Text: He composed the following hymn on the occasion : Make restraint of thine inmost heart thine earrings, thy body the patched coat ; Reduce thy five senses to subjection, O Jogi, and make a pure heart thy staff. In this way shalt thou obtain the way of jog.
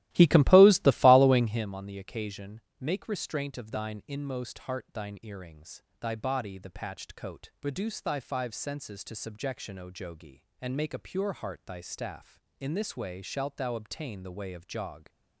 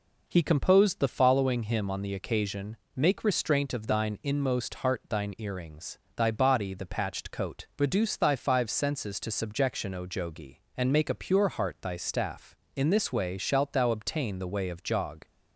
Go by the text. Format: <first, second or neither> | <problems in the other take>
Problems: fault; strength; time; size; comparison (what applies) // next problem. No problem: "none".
second | starts louder than the rest; strong; until 1.7 s; 15.5 dB